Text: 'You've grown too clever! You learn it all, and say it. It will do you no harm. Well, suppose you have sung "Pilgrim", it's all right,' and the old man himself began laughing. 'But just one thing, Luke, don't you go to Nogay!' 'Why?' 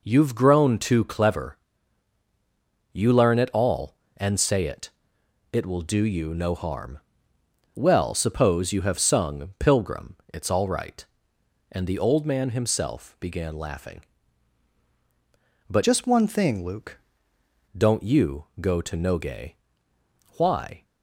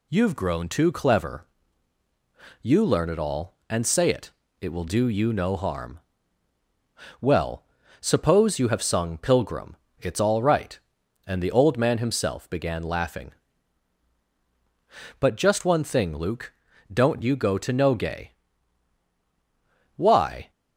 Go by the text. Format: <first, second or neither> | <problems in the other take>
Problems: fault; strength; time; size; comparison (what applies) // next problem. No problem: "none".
second | changes voice from "just" to "Luke"; from 15.8 to 16.9 s; 1.1 s long // pauses between "you" and "go"; slight; at 18.4 s; 0.16 s long